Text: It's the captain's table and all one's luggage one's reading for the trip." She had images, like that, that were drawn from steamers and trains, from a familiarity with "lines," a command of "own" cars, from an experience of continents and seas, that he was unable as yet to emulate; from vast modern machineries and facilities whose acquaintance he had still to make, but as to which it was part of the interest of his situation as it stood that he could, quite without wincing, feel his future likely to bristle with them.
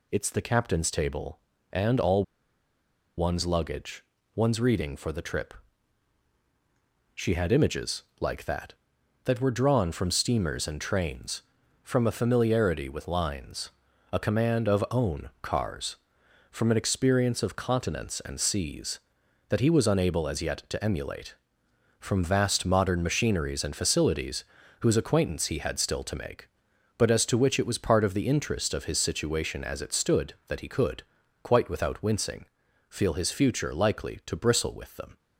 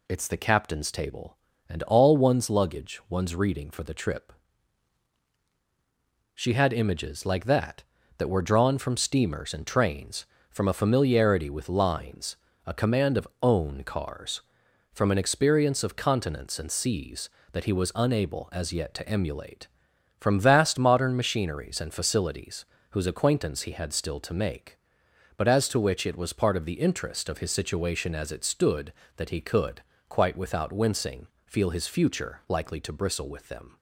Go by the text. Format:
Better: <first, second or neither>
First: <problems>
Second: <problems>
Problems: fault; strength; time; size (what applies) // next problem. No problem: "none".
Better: second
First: pauses between "all" and "one's"; noticeable; at 2.2 s; 0.94 s long // pauses between "luggage" and "one's"; slight; at 4.0 s; 0.30 s long // pauses between "facilities" and "whose"; slight; at 24.4 s; 0.36 s long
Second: pauses between "facilities" and "whose"; slight; at 22.6 s; 0.26 s long